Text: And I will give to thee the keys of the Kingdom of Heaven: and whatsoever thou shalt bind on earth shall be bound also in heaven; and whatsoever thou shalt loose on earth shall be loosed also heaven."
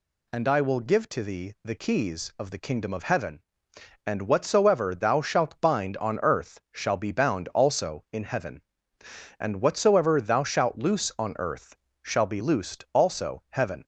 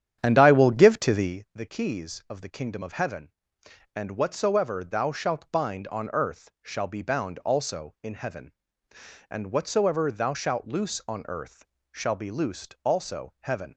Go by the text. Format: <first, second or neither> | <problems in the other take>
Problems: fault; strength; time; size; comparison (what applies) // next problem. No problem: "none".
first | starts louder than the rest; strong; until 1.4 s; 9.5 dB // pauses between "earth" and "shall"; slight; at 11.6 s; 0.26 s long; slight in the first